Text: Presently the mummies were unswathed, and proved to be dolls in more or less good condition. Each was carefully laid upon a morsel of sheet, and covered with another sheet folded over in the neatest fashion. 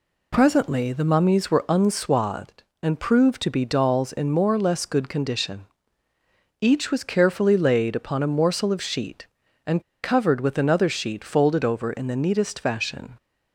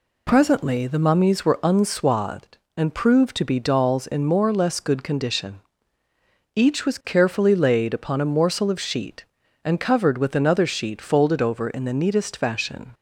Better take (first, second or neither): second